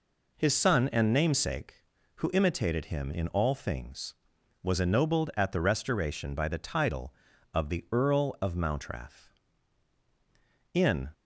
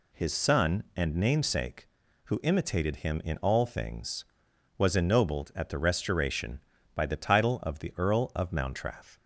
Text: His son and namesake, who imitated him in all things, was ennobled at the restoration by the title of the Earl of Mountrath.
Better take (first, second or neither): second